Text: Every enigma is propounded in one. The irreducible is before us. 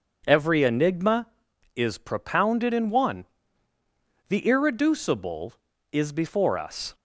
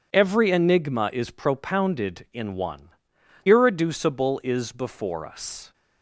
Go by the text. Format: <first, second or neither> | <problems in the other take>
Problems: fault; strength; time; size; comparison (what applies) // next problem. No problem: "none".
first | skips "The"; at 3.1 s